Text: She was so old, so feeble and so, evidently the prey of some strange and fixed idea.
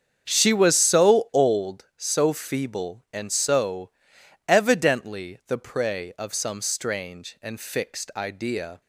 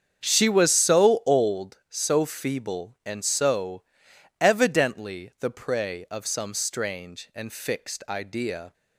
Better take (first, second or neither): neither